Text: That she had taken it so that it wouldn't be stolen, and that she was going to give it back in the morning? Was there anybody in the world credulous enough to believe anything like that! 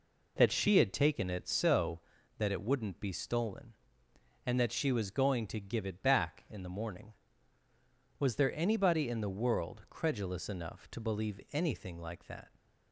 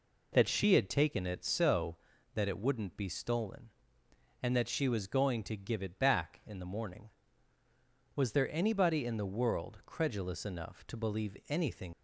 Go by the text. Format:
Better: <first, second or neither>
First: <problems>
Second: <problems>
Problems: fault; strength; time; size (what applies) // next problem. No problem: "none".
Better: first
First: none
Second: stops before "like that"; at 11.9 s